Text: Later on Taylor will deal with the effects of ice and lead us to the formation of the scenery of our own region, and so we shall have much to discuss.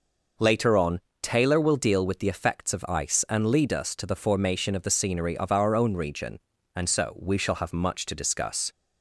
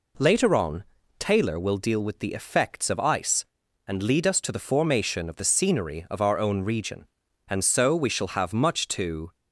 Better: first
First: pauses between "on" and "Taylor"; slight; at 1.0 s; 0.22 s long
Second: pauses between "on" and "Taylor"; slight; at 0.8 s; 0.34 s long // stops before "discuss"; at 9.3 s

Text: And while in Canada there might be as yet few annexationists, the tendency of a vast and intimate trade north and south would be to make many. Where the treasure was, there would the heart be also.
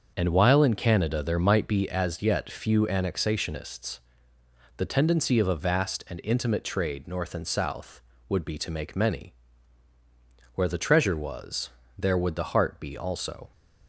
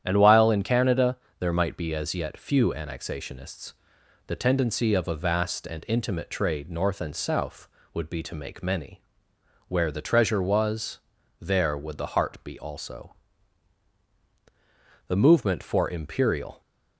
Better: first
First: starts louder than the rest; until 1.1 s; 6.5 dB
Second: starts louder than the rest; strong; until 1.0 s; 10 dB // pauses between "Canada" and "there"; slight; at 1.1 s; 0.22 s long // goes on to say "The movement for imperial"; from 15.0 s on; 1.5 s long

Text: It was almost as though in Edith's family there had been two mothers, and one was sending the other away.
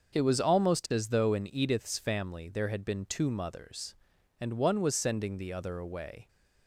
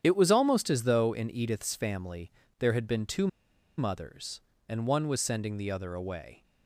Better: first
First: starts louder than the rest; until 1.1 s; 6.5 dB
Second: starts louder than the rest; strong; until 1.0 s; 9 dB // pauses between "family" and "there"; slight; at 2.3 s; 0.26 s long // pauses between "two" and "mothers"; noticeable; at 3.2 s; 0.50 s long

